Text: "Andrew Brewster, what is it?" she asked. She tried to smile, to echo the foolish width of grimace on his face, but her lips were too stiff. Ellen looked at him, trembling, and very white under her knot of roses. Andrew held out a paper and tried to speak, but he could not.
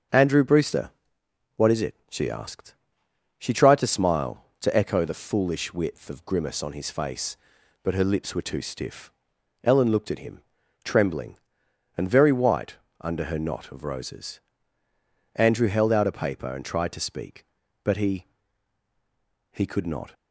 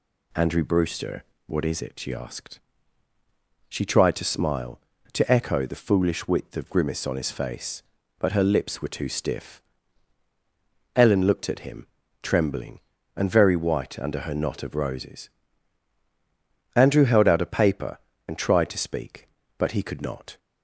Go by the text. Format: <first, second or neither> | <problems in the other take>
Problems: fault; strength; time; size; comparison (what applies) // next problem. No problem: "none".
second | starts louder than the rest; until 1.7 s; 7 dB // pauses between "white" and "under"; slight; at 12.7 s; 0.24 s long // says "he" twice; at 19.5 s